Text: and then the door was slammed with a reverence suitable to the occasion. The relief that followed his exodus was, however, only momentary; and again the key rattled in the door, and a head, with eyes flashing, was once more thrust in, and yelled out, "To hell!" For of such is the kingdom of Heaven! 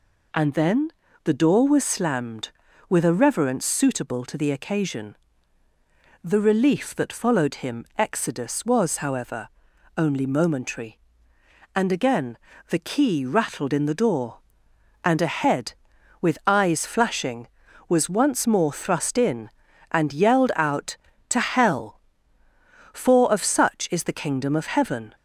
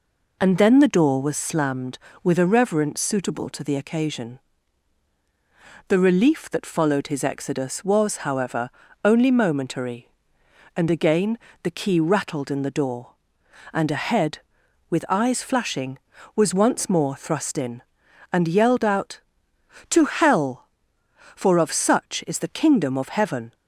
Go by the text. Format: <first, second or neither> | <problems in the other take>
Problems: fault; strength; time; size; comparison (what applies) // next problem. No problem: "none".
second | pauses between "then" and "the"; slight; at 0.8 s; 0.34 s long // says "him" for "his"; at 7.5 s // pauses between "again" and "the"; slight; at 12.3 s; 0.32 s long; slight in the second